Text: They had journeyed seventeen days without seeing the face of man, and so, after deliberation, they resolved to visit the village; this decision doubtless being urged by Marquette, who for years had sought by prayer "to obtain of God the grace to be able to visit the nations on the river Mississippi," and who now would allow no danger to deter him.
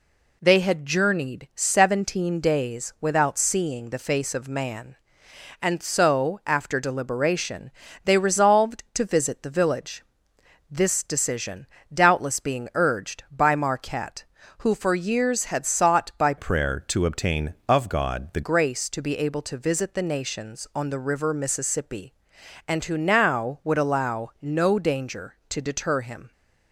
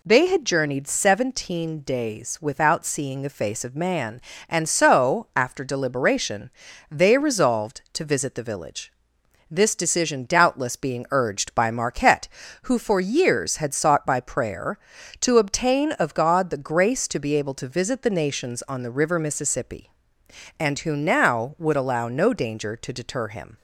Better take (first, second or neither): second